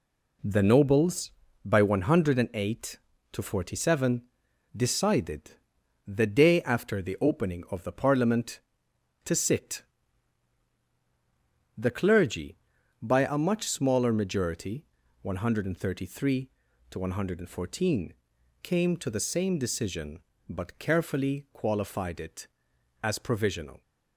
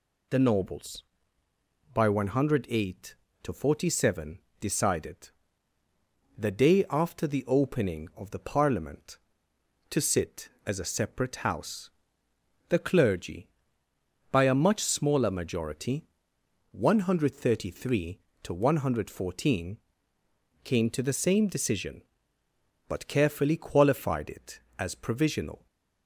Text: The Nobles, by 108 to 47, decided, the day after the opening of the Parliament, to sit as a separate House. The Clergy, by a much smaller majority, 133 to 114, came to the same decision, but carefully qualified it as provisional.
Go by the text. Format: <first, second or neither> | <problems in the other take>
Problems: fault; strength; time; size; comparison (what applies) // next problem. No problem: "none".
second | skips "as a separate House"; at 10.8 s